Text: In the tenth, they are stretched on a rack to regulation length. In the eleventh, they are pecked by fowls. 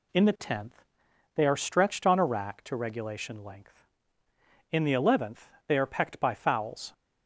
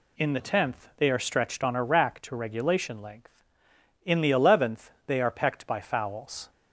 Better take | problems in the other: neither | none

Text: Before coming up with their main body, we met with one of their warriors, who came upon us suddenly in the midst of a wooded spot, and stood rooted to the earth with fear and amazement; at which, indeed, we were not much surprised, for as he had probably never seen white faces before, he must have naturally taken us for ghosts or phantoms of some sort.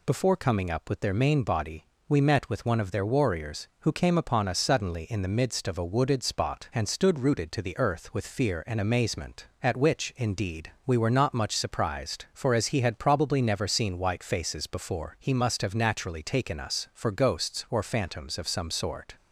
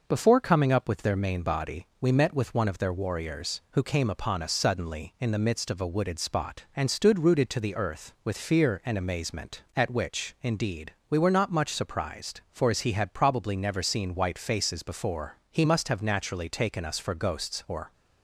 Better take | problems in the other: first | stops before "phantoms of some sort"; at 17.9 s

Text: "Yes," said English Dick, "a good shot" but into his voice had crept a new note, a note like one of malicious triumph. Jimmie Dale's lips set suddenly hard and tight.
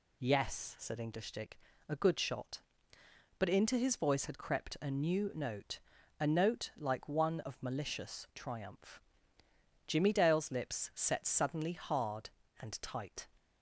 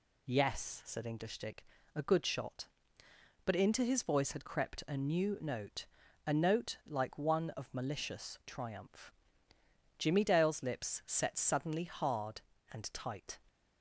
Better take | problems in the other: neither | none

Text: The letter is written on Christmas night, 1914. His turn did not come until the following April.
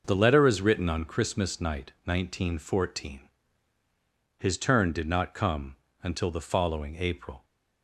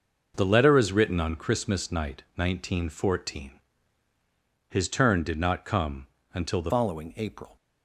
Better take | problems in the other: first | pauses between "come" and "until"; slight; at 6.0 s; 0.26 s long; slight in the first // changes voice at "following"; from 6.6 s on; 0.9 s long

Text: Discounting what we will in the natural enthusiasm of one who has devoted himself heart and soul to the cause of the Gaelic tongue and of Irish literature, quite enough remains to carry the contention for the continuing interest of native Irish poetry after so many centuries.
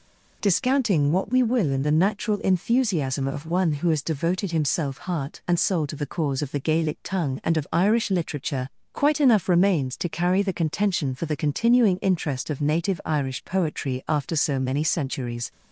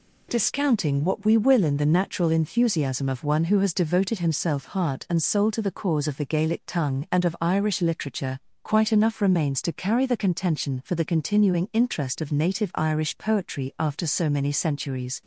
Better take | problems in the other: neither | none

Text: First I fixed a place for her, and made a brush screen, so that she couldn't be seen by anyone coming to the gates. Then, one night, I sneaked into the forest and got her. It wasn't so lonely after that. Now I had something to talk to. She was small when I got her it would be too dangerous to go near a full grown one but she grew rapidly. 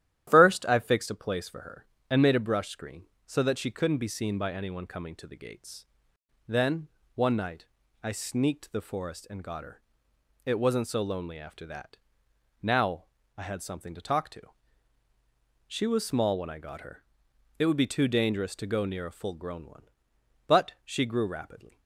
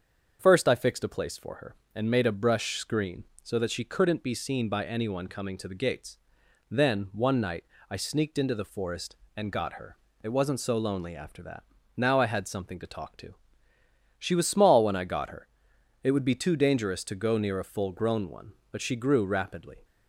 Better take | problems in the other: second | starts louder than the rest; strong; until 1.2 s; 12 dB; also in the second // skips "into"; at 8.7 s // pauses between "Now" and "I"; slight; at 13.0 s; 0.34 s long // pauses between "her" and "it"; noticeable; at 17.0 s; 0.58 s long; noticeable in the second

